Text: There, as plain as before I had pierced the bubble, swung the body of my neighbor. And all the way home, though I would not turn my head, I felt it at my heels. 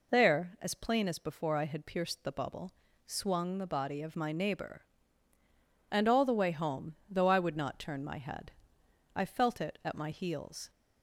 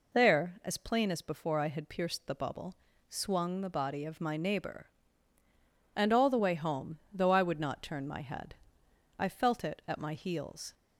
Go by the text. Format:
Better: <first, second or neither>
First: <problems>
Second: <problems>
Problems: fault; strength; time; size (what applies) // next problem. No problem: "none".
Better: neither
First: none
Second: none